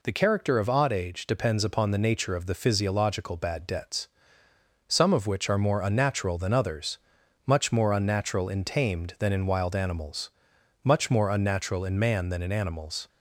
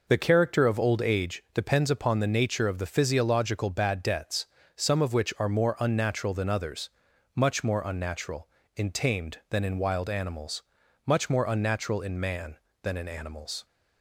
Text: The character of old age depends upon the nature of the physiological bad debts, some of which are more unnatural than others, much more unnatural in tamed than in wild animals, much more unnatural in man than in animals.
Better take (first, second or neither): second